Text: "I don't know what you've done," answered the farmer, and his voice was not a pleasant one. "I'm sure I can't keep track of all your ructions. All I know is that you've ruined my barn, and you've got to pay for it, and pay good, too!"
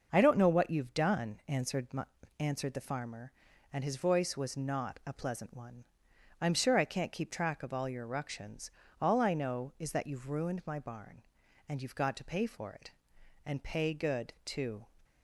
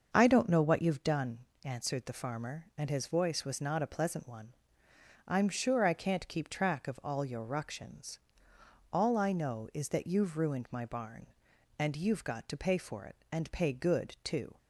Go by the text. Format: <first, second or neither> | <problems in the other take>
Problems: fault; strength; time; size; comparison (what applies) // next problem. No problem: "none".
second | starts louder than the rest; until 1.1 s; 6.5 dB; also in the second // says "answered" twice; at 2.3 s